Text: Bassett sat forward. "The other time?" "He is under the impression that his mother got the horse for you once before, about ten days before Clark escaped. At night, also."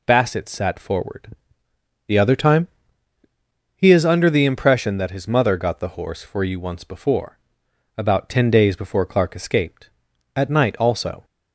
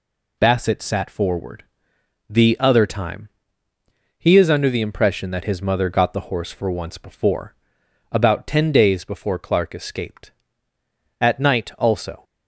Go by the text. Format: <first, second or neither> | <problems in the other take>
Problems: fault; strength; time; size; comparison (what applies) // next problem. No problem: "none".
first | skips "you"; at 6.6 s